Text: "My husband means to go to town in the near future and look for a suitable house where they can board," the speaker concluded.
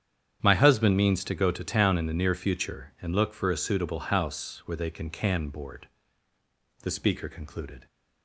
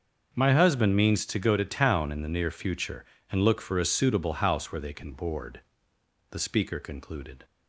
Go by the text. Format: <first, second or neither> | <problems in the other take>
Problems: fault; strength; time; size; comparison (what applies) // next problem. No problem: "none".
second | starts louder than the rest; strong; until 1.4 s; 9 dB; also in the second // says "can" twice; at 5.0 s